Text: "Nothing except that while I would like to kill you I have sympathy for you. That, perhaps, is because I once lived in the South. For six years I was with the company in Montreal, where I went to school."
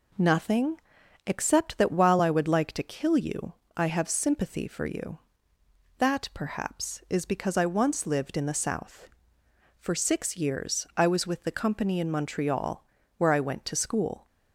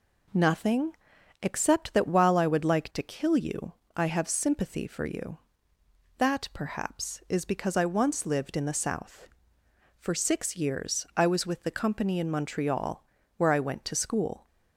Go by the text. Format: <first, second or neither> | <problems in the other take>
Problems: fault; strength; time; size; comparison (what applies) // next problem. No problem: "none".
neither | pauses between "Nothing" and "except"; noticeable; the same in both // pauses between "you" and "I"; slight; the same in both